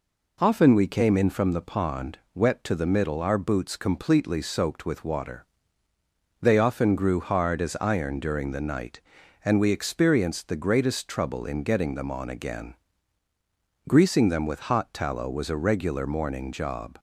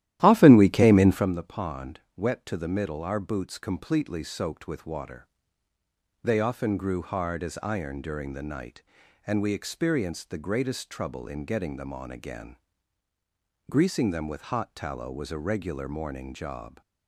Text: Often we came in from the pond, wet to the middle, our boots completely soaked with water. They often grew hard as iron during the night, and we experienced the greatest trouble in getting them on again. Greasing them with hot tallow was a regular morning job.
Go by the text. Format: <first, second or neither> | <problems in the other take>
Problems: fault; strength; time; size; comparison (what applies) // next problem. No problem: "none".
first | starts louder than the rest; strong; until 1.3 s; 13.5 dB